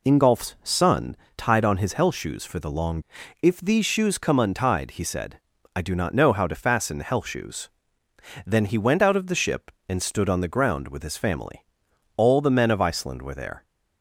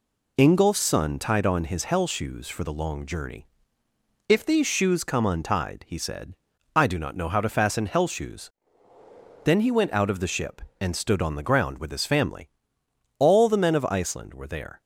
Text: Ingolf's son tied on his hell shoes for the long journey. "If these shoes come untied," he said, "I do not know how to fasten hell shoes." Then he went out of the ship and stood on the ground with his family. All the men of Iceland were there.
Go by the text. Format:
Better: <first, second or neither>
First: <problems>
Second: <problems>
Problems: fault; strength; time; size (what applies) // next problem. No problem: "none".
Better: second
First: pauses between "son" and "tied"; slight; at 1.1 s; 0.22 s long // skips "journey"; at 3.2 s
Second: none